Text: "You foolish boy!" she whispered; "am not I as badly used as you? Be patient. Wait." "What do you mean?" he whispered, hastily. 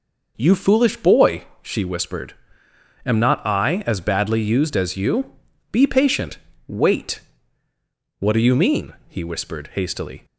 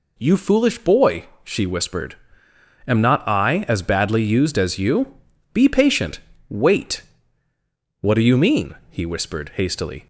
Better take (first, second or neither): second